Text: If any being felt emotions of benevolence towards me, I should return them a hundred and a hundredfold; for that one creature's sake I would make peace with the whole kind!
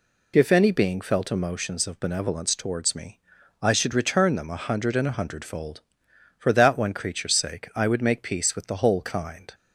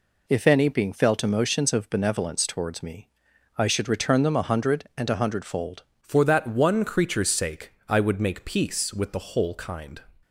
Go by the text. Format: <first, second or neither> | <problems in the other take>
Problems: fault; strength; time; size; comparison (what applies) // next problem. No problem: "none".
first | changes voice at "for"; from 6.0 s on; 4.0 s long // pauses between "sake" and "I"; slight; at 7.7 s; 0.16 s long